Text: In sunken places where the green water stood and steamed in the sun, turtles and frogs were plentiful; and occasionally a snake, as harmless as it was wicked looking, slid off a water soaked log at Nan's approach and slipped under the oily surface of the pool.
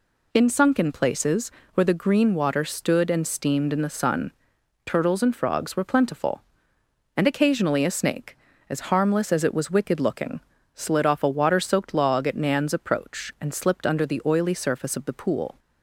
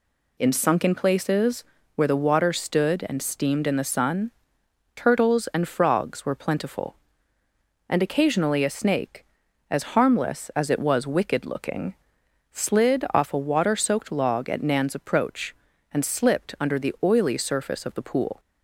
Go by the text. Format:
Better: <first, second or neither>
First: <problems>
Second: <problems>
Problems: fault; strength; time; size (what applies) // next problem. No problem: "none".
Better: first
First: pauses between "places" and "where"; slight; at 1.5 s; 0.24 s long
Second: pauses between "places" and "where"; slight; at 1.6 s; 0.32 s long // skips "green"; at 2.1 s